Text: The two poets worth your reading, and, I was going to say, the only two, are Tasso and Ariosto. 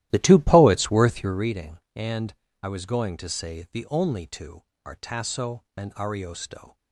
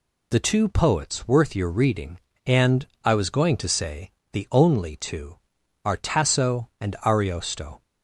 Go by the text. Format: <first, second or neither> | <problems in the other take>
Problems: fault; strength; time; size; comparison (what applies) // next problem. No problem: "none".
second | starts louder than the rest; strong; until 1.5 s; 14 dB